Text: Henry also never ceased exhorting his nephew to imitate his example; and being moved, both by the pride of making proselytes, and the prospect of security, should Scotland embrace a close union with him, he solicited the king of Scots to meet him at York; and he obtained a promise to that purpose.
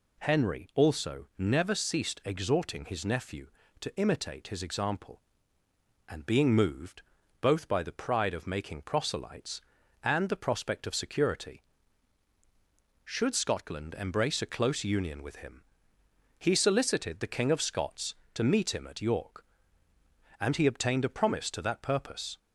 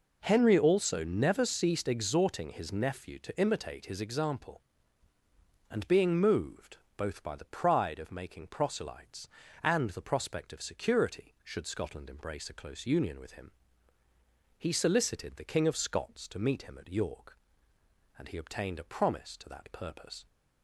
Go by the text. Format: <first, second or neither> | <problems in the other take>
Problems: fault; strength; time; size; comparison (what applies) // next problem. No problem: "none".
neither | none